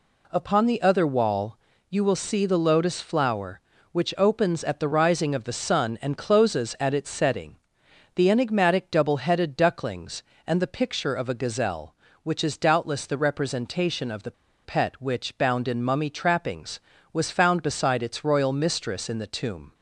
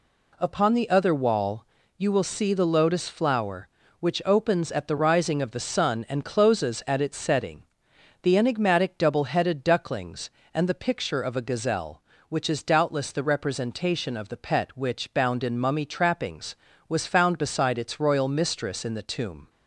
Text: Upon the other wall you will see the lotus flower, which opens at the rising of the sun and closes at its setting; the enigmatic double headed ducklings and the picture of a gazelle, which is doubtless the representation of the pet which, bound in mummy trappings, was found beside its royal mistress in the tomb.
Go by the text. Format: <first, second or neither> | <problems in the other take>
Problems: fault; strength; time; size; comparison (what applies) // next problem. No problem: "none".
second | pauses between "wall" and "you"; slight; at 1.5 s; 0.32 s long; slight in the second // pauses between "the" and "pet"; slight; at 14.3 s; 0.32 s long